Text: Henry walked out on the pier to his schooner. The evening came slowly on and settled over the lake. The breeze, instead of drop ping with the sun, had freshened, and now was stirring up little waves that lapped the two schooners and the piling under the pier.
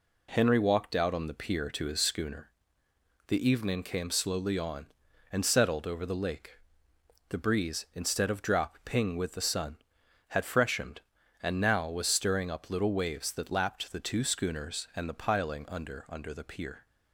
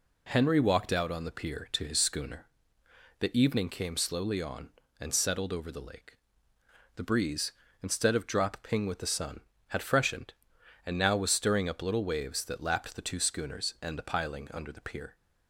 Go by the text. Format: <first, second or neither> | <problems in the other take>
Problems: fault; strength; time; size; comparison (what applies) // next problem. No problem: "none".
second | says "under" twice; at 16.0 s